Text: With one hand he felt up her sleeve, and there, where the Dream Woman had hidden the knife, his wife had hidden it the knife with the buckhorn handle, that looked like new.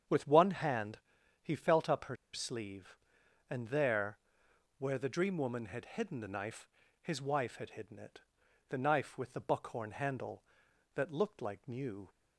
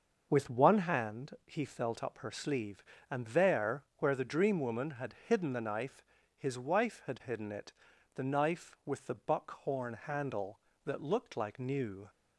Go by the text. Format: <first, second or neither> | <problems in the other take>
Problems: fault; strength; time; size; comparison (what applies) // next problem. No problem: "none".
second | starts louder than the rest; strong; until 1.5 s; 8 dB; noticeable in the second // pauses between "hand" and "he"; at 0.9 s; 0.42 s long // pauses between "her" and "sleeve"; slight; at 2.1 s; 0.17 s long // pauses between "it" and "the"; noticeable; at 8.2 s; 0.48 s long; also in the second